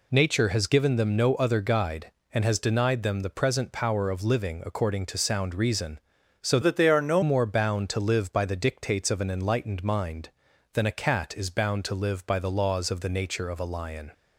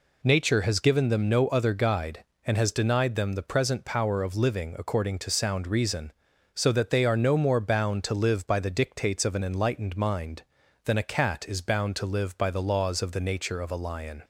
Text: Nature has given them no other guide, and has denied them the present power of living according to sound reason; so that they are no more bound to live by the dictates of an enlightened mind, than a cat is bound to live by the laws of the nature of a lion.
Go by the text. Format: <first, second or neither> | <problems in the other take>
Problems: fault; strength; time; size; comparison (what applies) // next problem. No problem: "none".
second | changes voice from "that" to "no"; from 6.6 to 7.2 s; 0.6 s long